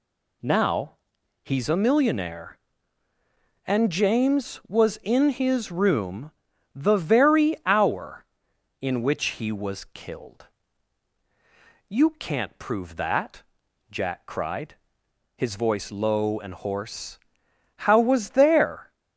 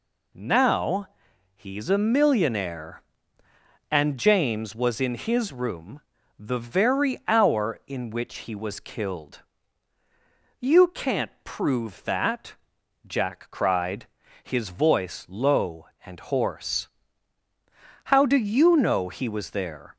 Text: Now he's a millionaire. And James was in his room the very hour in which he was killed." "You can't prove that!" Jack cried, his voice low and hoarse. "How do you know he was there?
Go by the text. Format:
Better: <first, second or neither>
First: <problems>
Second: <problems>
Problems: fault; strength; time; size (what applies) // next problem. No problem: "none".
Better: second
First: pauses between "Now" and "he's"; noticeable; at 0.9 s; 0.50 s long // pauses between "room" and "the"; at 6.3 s; 0.42 s long // skips "do you know he"; at 17.9 s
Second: pauses between "Now" and "he's"; noticeable; at 1.0 s; 0.46 s long // pauses between "room" and "the"; at 6.0 s; 0.38 s long